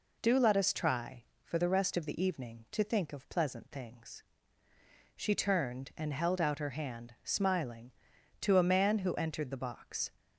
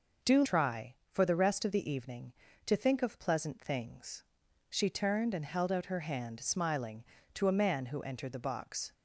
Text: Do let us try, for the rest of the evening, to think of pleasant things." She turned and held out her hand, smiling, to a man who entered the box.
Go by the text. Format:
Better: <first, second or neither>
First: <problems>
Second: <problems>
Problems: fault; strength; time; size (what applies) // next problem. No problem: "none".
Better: first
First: none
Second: skips "let us"; at 0.4 s